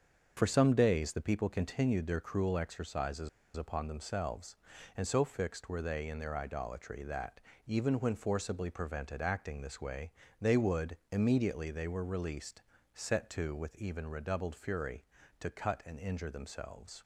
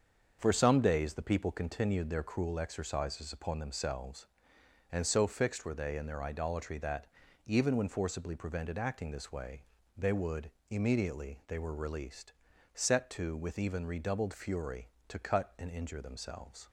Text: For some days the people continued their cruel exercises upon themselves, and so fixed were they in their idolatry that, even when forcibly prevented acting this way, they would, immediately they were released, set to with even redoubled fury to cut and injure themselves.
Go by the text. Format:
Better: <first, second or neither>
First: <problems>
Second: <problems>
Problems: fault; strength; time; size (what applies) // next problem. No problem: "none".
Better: second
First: starts louder than the rest; until 1.3 s; 6.5 dB // pauses between "exercises" and "upon"; slight; at 3.2 s; 0.27 s long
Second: starts louder than the rest; until 1.4 s; 7 dB